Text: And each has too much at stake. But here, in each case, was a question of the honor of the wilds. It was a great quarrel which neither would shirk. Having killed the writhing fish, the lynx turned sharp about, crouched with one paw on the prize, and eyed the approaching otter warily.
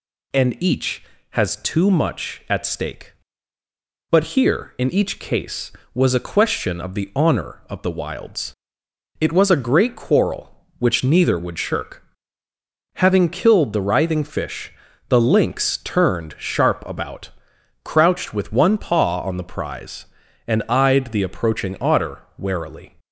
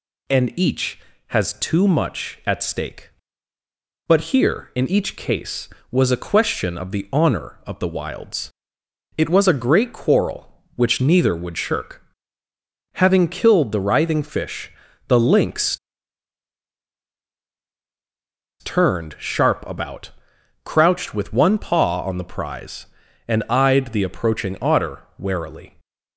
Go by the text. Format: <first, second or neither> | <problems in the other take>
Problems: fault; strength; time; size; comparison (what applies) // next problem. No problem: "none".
first | pauses between "lynx" and "turned"; strong; at 15.7 s; 2.8 s long // pauses between "otter" and "warily"; slight; at 25.0 s; 0.16 s long; slight in the first